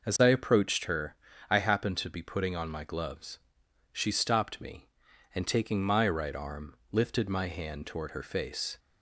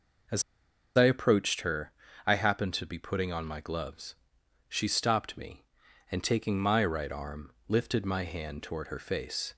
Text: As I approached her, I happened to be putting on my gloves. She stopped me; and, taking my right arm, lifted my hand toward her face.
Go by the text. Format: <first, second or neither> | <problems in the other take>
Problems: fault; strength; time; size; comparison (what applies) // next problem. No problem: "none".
first | pauses between "As" and "I"; noticeable; at 0.4 s; 0.54 s long